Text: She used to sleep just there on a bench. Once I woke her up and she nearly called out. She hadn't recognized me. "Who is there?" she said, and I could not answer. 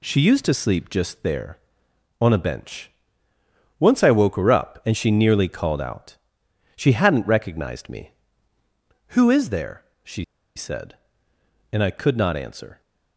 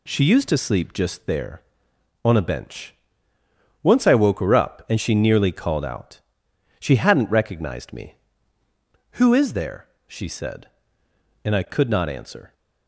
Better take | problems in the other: second | pauses between "she" and "said"; slight; at 10.2 s; 0.31 s long

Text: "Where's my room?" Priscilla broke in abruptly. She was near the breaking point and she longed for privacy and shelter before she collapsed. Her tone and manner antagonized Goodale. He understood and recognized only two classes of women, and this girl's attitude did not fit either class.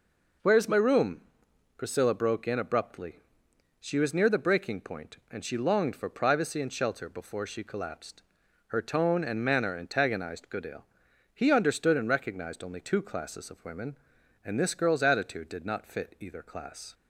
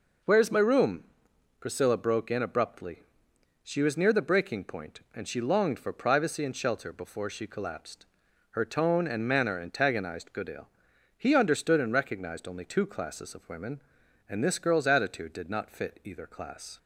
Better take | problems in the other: neither | none

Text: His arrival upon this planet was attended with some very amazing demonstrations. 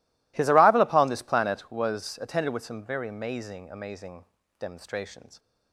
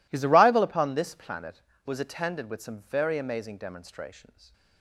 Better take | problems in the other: second | says "amazing" twice; at 3.7 s

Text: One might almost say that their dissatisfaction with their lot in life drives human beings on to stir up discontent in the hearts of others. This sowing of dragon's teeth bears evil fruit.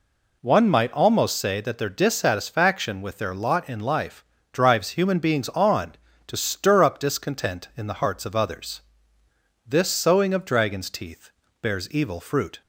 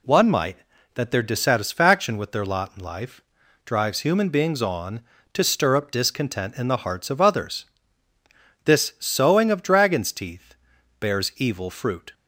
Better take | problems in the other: first | skips "almost say"; at 0.7 s // pauses between "life" and "drives"; at 3.2 s; 0.44 s long; slight in the first // pauses between "teeth" and "bears"; at 10.5 s; 0.44 s long; slight in the first

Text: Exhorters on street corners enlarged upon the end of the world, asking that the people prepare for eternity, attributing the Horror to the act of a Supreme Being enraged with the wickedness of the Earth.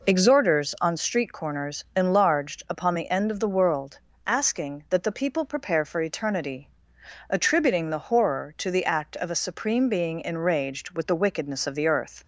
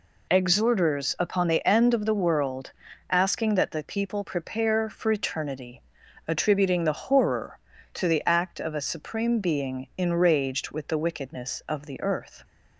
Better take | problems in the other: first | skips "on street corners enlarged"; at 1.1 s

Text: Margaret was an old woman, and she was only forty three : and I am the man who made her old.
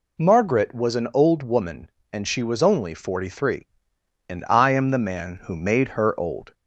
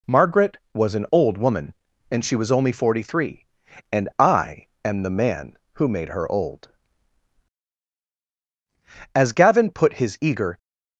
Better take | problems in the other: first | pauses between "I" and "am"; slight; at 4.6 s; 0.18 s long // goes on to say "As Gavin put his eager"; from 9.1 s on; 1.4 s long

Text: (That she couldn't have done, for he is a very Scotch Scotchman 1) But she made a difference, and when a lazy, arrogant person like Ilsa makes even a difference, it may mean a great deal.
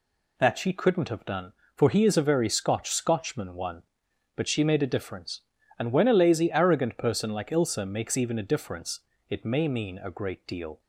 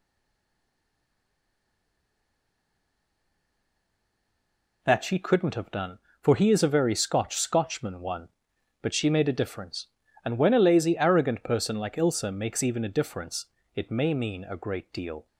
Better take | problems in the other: first | stays silent before the first word; strong; until 4.8 s; 4.8 s long

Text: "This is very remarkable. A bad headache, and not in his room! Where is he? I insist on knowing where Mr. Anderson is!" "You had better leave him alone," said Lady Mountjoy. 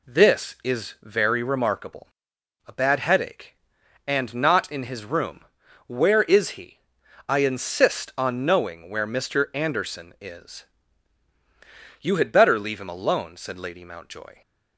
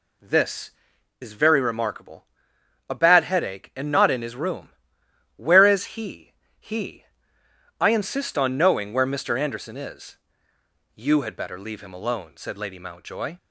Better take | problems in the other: first | says "he" twice; at 6.5 s

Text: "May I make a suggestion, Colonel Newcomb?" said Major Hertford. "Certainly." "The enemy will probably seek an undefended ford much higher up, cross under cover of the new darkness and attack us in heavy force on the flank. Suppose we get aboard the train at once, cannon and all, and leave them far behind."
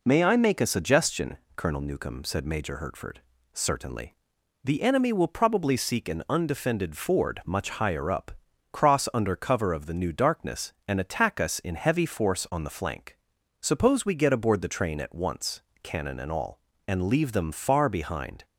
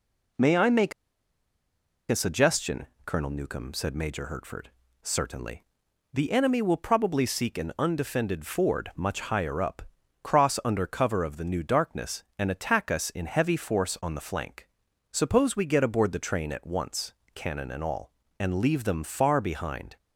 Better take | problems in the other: first | pauses between "make" and "a"; at 0.9 s; 1.1 s long

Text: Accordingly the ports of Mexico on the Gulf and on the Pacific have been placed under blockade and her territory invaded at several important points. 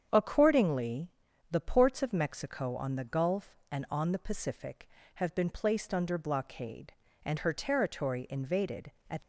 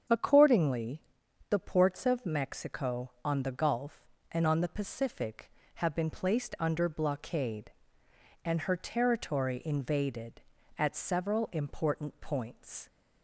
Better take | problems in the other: second | starts louder than the rest; strong; until 1.1 s; 8 dB; strong in the second // pauses between "Accordingly" and "the"; at 1.1 s; 0.40 s long; noticeable in the second // stops before "several important points"; at 9.2 s

